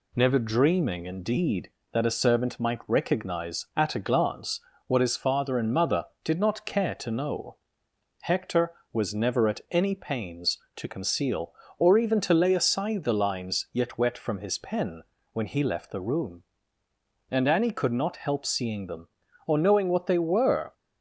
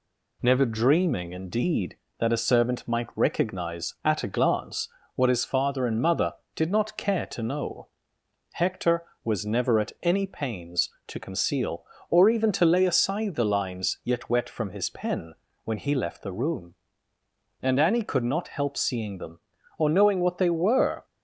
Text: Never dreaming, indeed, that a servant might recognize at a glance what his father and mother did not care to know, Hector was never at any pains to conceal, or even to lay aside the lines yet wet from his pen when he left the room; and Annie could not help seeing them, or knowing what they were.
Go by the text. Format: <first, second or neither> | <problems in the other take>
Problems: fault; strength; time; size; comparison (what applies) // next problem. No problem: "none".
neither | pauses between "glance" and "what"; slight; the same in both // pauses between "pen" and "when"; slight; the same in both